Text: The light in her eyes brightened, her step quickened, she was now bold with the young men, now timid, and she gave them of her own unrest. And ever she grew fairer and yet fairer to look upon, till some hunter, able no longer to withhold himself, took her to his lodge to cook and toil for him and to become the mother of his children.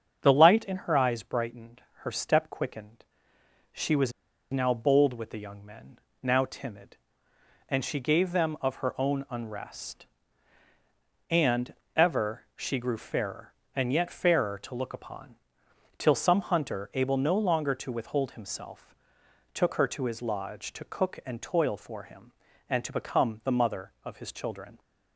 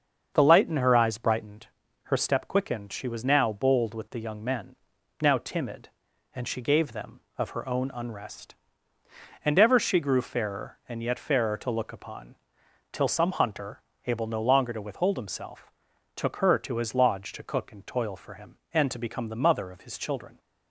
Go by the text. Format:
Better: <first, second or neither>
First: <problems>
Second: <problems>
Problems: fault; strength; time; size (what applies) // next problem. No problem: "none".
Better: second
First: starts louder than the rest; until 1.2 s; 7 dB // pauses between "was" and "now"; at 4.1 s; 0.41 s long // pauses between "And" and "ever"; slight; at 11.7 s; 0.24 s long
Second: starts louder than the rest; until 1.3 s; 7 dB